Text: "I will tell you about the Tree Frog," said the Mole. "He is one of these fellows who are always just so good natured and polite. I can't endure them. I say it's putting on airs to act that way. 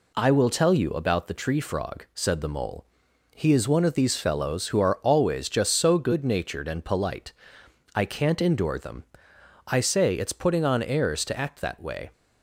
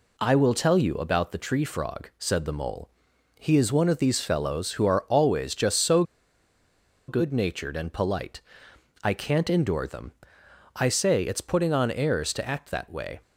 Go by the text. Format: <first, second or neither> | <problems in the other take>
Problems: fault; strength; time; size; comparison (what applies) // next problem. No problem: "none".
first | pauses between "so" and "good"; at 6.0 s; 1.0 s long